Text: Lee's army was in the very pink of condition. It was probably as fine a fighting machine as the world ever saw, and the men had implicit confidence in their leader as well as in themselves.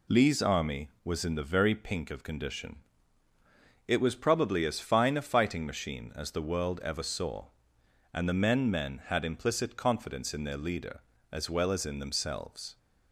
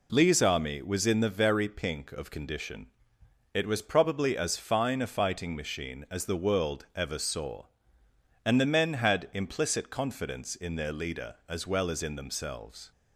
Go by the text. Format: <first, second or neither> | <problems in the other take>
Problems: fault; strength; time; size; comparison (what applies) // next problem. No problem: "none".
second | says "men" twice; at 8.6 s